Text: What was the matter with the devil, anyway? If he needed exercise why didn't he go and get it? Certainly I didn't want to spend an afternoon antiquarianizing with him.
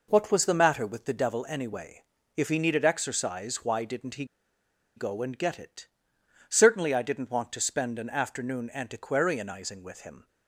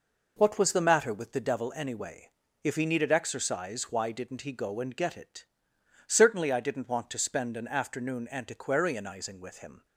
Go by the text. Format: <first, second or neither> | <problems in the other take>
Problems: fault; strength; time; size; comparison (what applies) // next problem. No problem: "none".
second | pauses between "he" and "go"; noticeable; at 4.2 s; 0.72 s long